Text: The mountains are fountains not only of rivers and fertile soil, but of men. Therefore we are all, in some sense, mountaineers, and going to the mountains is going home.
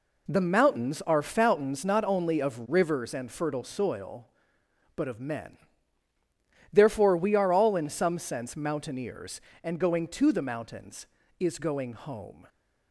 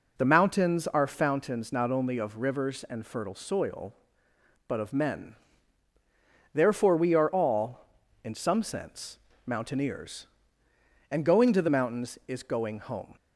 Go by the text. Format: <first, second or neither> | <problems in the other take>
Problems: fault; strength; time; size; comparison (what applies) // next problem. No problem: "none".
neither | none